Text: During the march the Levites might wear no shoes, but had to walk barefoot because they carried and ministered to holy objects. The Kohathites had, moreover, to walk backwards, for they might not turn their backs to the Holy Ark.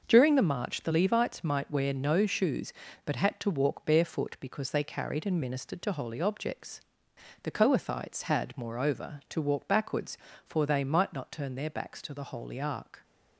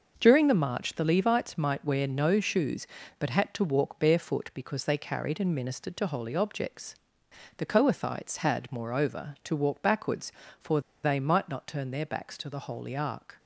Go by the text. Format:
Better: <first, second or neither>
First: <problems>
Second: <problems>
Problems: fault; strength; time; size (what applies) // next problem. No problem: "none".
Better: first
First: none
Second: pauses between "for" and "they"; slight; at 10.7 s; 0.24 s long